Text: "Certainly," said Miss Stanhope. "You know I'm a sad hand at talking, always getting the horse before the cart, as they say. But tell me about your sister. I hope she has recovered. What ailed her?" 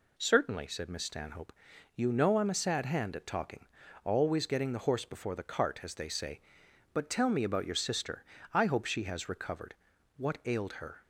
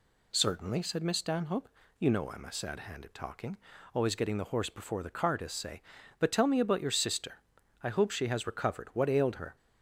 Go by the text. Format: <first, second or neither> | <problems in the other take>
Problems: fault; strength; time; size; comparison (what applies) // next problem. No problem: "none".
first | skips "they"; at 5.5 s